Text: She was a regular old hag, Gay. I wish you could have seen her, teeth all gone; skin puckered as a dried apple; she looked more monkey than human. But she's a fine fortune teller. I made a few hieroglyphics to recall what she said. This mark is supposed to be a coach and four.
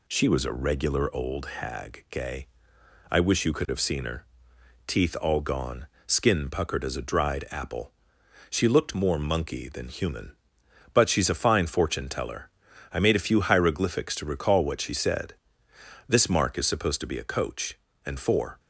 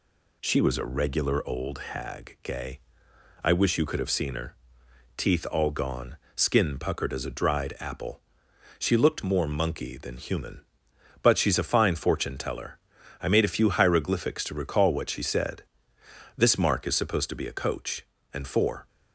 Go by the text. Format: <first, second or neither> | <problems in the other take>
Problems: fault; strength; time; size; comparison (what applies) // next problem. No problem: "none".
neither | none